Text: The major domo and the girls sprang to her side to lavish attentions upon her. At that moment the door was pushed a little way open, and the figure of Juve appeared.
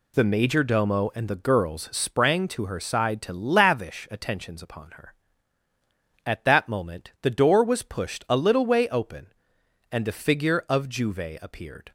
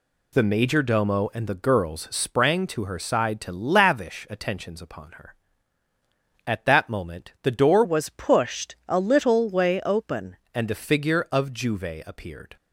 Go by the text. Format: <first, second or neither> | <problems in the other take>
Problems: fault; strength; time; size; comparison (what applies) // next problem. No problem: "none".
first | changes voice from "was" to "open"; from 7.8 to 10.3 s; 2.5 s long